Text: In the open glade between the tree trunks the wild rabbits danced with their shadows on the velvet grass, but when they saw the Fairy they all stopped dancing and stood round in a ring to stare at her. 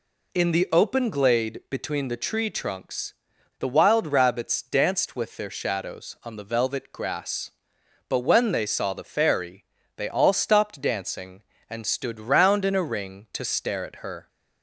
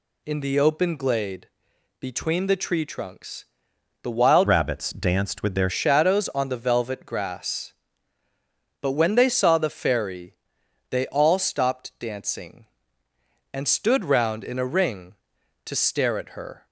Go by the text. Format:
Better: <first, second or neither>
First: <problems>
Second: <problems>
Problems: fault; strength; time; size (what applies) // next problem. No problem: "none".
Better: first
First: pauses between "trunks" and "the"; at 3.1 s; 0.44 s long // pauses between "Fairy" and "they"; slight; at 9.6 s; 0.32 s long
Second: pauses between "glade" and "between"; noticeable; at 1.4 s; 0.52 s long // pauses between "trunks" and "the"; noticeable; at 3.4 s; 0.60 s long // changes voice from "rabbits" to "their"; from 4.4 to 5.7 s; 1.3 s long // pauses between "Fairy" and "they"; noticeable; at 10.3 s; 0.56 s long